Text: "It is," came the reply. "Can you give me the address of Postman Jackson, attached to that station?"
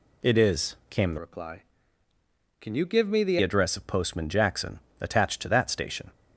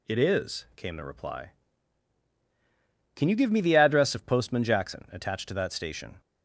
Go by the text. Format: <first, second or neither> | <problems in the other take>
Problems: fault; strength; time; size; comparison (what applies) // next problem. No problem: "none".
second | changes voice from "reply" to "the"; from 1.1 to 3.3 s; 2.2 s long